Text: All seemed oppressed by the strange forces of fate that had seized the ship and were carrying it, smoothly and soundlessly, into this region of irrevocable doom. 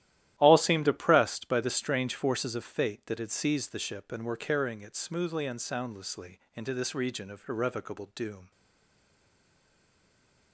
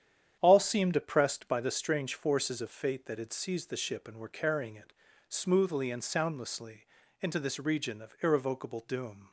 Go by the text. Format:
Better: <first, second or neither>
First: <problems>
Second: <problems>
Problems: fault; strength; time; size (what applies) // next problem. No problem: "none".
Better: second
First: starts louder than the rest; strong; until 1.3 s; 13 dB // stays silent after the last word; noticeable; from 8.5 s on; 2.0 s long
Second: starts louder than the rest; strong; until 1.4 s; 9.5 dB